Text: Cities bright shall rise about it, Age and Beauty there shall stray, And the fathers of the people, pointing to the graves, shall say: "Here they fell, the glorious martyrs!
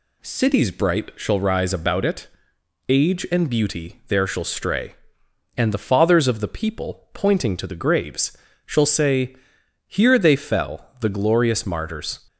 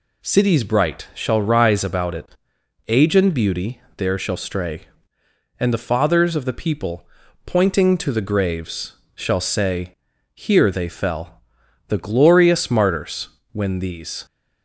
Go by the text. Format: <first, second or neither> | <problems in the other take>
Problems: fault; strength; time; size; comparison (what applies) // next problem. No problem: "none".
first | pauses between "Beauty" and "there"; slight; at 3.8 s; 0.16 s long // goes on to say "when these"; noticeable; from 13.5 s on; 0.74 s long